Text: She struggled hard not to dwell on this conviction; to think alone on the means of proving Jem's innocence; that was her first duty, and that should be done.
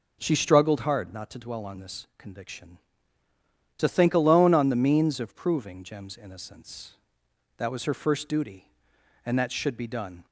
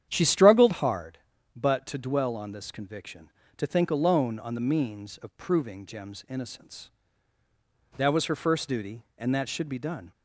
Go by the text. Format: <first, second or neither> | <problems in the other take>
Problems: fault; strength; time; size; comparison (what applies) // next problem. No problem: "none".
first | starts louder than the rest; strong; until 1.0 s; 9.5 dB // says "but" for "not"; at 1.5 s